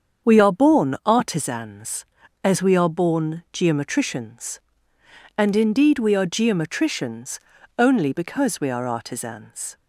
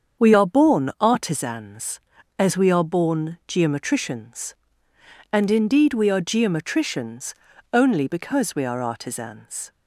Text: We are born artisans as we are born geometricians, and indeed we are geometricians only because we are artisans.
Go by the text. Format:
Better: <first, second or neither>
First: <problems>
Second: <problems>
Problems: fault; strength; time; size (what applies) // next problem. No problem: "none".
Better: neither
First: starts louder than the rest; strong; until 1.3 s; 7 dB // pauses between "geometricians" and "only"; slight; at 7.4 s; 0.36 s long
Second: starts louder than the rest; strong; until 1.3 s; 7 dB // pauses between "geometricians" and "only"; slight; at 7.3 s; 0.36 s long